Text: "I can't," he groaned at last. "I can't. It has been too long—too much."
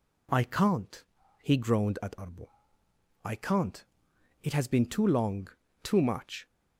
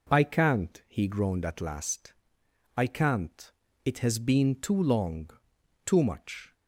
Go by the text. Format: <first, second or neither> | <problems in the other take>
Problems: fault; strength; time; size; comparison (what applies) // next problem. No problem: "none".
second | says "arbo" for "last"; at 2.1 s